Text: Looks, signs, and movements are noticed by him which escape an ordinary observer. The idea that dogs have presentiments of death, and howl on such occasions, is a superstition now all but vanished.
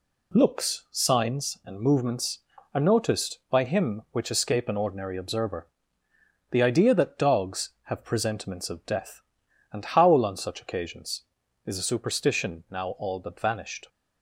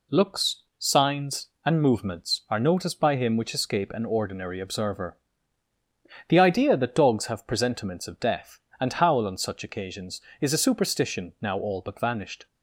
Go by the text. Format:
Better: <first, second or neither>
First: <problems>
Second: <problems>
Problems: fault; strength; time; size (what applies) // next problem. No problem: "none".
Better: neither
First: none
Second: none